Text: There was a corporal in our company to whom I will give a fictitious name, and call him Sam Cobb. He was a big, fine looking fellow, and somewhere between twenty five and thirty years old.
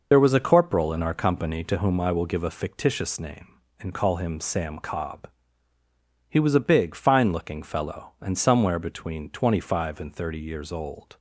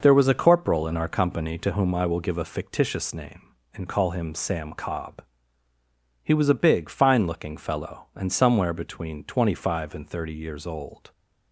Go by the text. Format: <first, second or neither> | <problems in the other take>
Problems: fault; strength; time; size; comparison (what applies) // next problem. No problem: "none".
second | loses the start of "There"; at 0.1 s; 55 ms